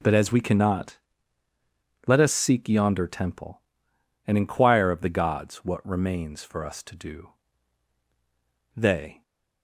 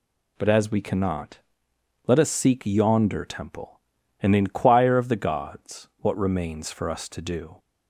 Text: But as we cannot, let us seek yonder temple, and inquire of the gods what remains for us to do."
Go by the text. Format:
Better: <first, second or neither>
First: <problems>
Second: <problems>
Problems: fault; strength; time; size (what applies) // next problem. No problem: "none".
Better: second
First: goes on to say "They"; slight; from 8.7 s on; 0.48 s long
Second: none